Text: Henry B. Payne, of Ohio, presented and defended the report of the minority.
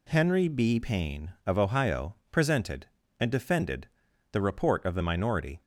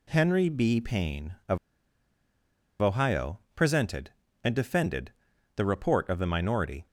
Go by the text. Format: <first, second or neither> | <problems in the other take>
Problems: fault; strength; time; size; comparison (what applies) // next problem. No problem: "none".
first | pauses between "of" and "Ohio"; at 1.5 s; 1.2 s long // pauses between "defended" and "the"; at 5.1 s; 0.42 s long; also in the first